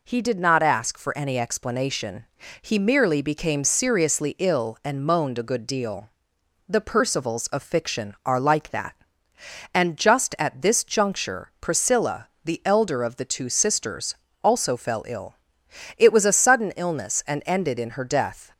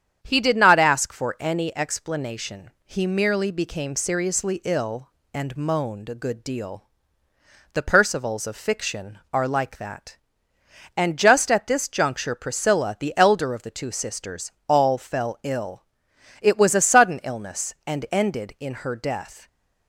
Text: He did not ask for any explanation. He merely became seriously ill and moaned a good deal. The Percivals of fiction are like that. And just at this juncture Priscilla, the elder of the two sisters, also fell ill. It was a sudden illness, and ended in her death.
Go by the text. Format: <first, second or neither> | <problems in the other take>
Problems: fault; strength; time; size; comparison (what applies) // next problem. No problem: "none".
first | starts louder than the rest; strong; until 1.2 s; 8.5 dB // says "all" for "also"; at 14.6 s